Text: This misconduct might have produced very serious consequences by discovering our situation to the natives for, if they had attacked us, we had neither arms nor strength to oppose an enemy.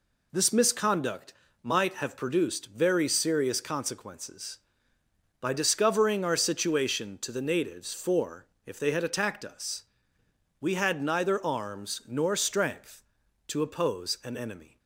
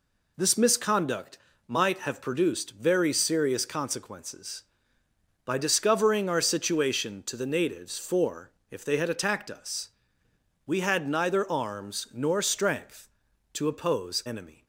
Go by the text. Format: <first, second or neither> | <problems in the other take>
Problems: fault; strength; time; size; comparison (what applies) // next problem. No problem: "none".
first | pauses between "misconduct" and "might"; slight; at 1.3 s; 0.30 s long; slight in the first // skips "an"; at 14.2 s